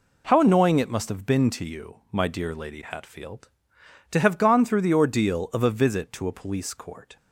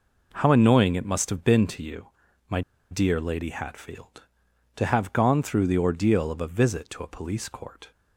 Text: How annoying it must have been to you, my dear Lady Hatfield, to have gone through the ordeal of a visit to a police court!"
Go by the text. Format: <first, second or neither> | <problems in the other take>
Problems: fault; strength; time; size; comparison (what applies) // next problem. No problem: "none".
first | pauses between "my" and "dear"; slight; at 2.6 s; 0.29 s long